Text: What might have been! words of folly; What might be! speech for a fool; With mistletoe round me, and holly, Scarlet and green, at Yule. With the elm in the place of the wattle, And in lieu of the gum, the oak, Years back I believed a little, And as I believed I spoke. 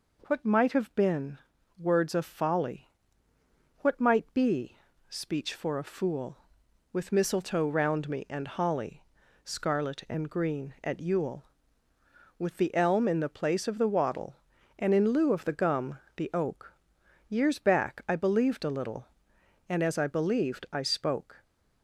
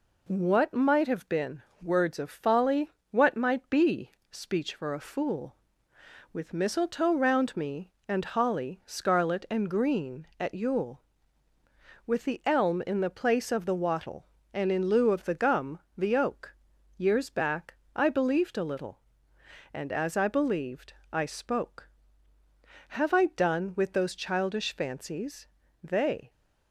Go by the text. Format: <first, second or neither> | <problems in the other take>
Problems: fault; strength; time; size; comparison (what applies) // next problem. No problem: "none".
first | pauses between "back" and "I"; slight; at 17.7 s; 0.20 s long // pauses between "believed" and "I"; slight; at 20.9 s; 0.18 s long // goes on to say "Have I done with those childish fancies They"; strong; from 22.8 s on; 3.4 s long